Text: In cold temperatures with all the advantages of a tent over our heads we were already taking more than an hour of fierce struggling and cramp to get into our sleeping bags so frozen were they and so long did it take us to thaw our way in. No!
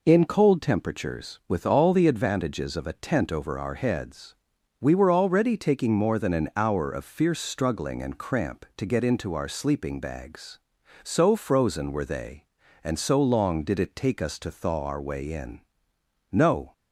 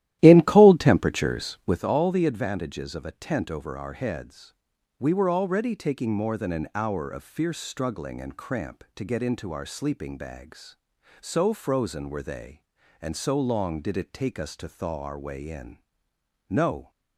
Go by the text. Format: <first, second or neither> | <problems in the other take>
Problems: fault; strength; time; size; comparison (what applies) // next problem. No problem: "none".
first | starts louder than the rest; strong; until 1.9 s; 13.5 dB // pauses between "heads" and "we"; noticeable; at 4.5 s; 0.46 s long; noticeable in the first